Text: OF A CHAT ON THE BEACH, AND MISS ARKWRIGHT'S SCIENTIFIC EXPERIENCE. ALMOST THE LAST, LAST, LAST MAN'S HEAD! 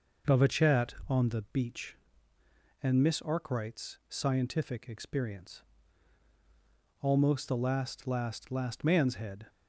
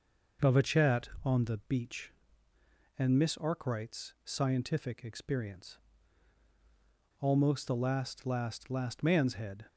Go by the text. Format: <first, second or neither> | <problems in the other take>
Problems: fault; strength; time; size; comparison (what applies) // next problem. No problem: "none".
neither | none